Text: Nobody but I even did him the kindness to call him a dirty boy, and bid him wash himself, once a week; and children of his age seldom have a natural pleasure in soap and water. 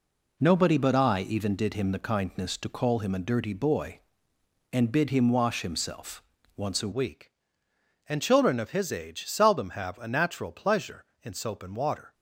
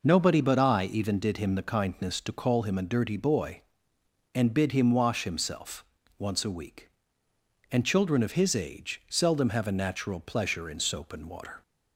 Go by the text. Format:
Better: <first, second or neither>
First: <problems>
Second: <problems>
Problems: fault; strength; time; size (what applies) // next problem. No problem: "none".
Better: second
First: changes voice at "week"; from 6.9 s on; 5.2 s long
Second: none